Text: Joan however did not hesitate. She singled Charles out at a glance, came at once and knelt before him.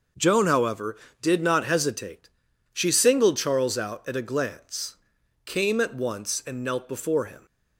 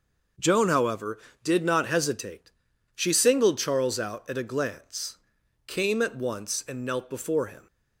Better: neither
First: starts louder than the rest; noticeable; until 1.4 s; 6 dB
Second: starts louder than the rest; noticeable; until 1.6 s; 6 dB

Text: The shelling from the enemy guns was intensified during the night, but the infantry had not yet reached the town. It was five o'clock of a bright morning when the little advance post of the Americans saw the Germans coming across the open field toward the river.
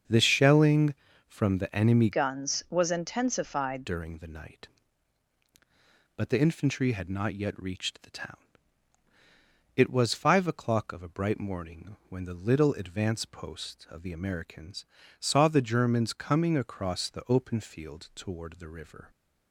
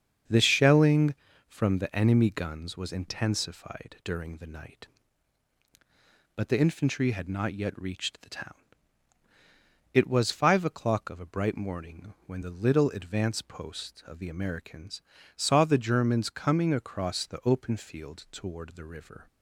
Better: second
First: starts louder than the rest; until 1.4 s; 7 dB // changes voice from "guns" to "intensified"; from 2.1 to 3.8 s; 1.7 s long // pauses between "Americans" and "saw"; slight; at 14.8 s; 0.32 s long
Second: starts louder than the rest; until 1.6 s; 7 dB // pauses between "Americans" and "saw"; slight; at 15.0 s; 0.32 s long

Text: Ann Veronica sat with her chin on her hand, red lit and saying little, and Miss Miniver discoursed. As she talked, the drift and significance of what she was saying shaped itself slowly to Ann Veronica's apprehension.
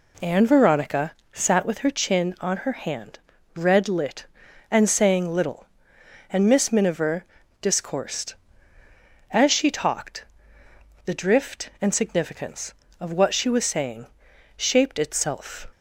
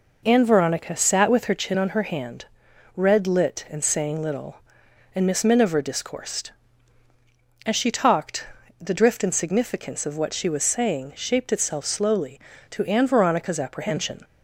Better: second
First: pauses between "Veronica" and "sat"; slight; at 1.1 s; 0.22 s long // pauses between "Miniver" and "discoursed"; slight; at 7.2 s; 0.36 s long // pauses between "saying" and "shaped"; noticeable; at 14.0 s; 0.50 s long // stops before "slowly to Ann Veronica's apprehension"; at 15.7 s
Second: none

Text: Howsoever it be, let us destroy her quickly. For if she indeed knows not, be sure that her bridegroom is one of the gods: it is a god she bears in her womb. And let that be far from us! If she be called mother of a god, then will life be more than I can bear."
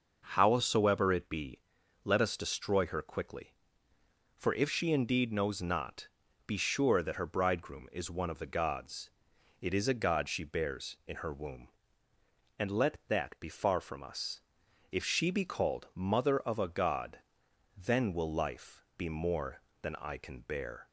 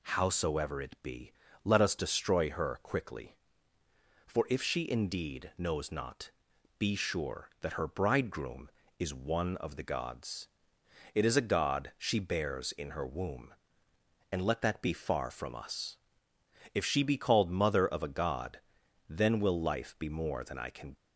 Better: first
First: none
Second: stops before "bear"; at 20.9 s

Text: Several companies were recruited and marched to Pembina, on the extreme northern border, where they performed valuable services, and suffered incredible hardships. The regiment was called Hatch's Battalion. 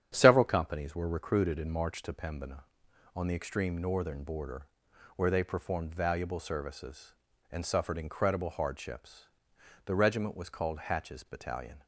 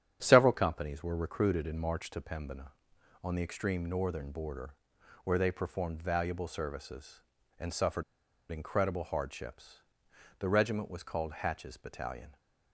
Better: first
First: starts louder than the rest; strong; until 1.1 s; 9 dB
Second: starts louder than the rest; strong; until 1.2 s; 9 dB // pauses between "suffered" and "incredible"; noticeable; at 8.0 s; 0.47 s long

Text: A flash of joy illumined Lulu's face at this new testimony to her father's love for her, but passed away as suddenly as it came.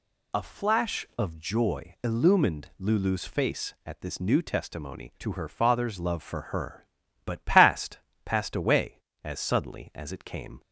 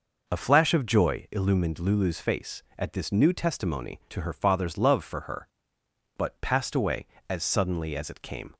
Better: second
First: says "passed" twice; at 8.2 s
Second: none

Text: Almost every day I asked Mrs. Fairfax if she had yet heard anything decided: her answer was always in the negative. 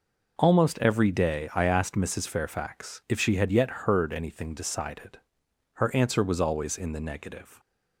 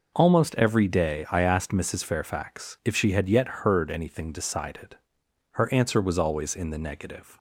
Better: neither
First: none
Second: none

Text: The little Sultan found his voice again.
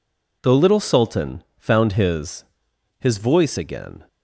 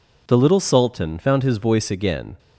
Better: second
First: pauses between "Sultan" and "found"; slight; at 1.4 s; 0.15 s long // says "his" twice; at 3.0 s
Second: none

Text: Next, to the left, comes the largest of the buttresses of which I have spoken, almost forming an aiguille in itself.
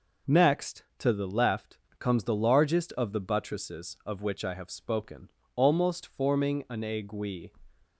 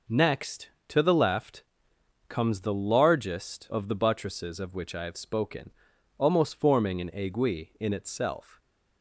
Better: second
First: stops before "in itself"; at 7.8 s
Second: none

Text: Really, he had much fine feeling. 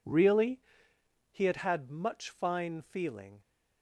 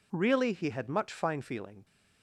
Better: second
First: says "had" twice; at 1.5 s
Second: none

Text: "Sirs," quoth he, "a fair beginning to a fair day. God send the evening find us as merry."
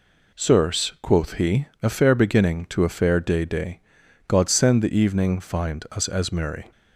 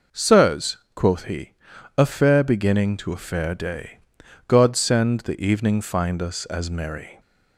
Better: second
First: says "day" twice; at 3.4 s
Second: none

